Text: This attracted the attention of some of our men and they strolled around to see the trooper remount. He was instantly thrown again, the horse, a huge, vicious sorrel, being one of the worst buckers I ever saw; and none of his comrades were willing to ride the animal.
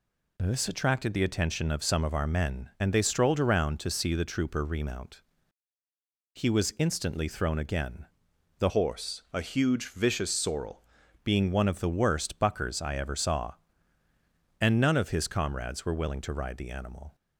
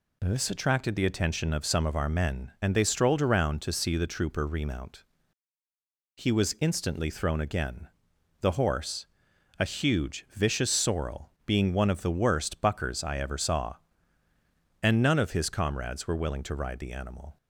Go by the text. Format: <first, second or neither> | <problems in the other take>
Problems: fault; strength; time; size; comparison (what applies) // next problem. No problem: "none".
second | changes voice from "horse" to "sorrel"; from 8.6 to 10.8 s; 2.2 s long